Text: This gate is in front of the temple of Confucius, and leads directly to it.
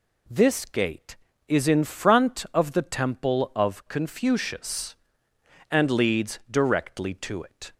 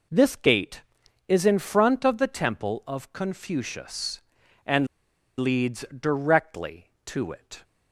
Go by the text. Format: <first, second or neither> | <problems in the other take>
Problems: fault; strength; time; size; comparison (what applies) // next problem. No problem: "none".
first | pauses between "and" and "leads"; noticeable; at 4.8 s; 0.52 s long